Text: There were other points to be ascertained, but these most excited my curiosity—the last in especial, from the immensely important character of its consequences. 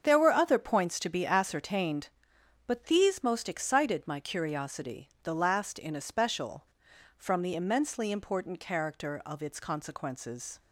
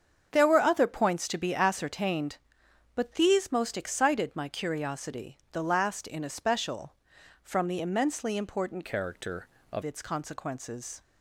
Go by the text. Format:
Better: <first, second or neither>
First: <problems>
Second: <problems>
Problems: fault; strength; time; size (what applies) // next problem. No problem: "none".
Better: first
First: starts louder than the rest; strong; until 1.0 s; 7 dB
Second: starts louder than the rest; strong; until 1.3 s; 7.5 dB // changes voice from "character" to "of"; from 8.8 to 9.8 s; 1.0 s long